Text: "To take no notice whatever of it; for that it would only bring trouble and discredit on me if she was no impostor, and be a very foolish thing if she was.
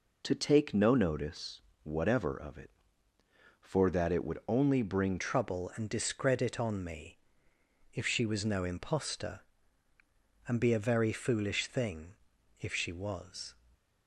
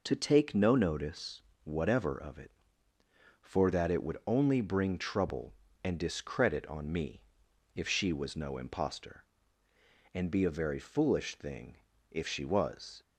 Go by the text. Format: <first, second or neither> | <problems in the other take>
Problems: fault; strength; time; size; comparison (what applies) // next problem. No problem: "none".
second | pauses between "notice" and "whatever"; slight; at 1.6 s; 0.24 s long; slight in the second // changes voice at "trouble"; from 5.1 s on; 8.4 s long // pauses between "me" and "if"; noticeable; at 7.1 s; 0.74 s long; noticeable in the second // pauses between "thing" and "if"; noticeable; at 12.1 s; 0.48 s long; slight in the second // stays silent after the last word; slight; from 13.5 s on; 0.5 s long